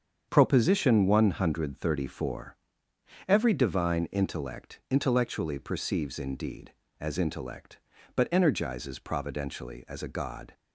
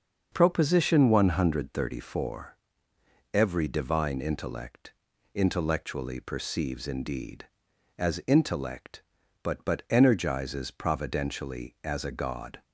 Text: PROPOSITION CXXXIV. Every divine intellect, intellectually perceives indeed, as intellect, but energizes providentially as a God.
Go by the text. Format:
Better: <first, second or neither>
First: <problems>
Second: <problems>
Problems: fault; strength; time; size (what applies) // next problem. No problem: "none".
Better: first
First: starts louder than the rest; strong; until 1.3 s; 7.5 dB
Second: starts louder than the rest; until 1.3 s; 6.5 dB // says "but" twice; at 9.6 s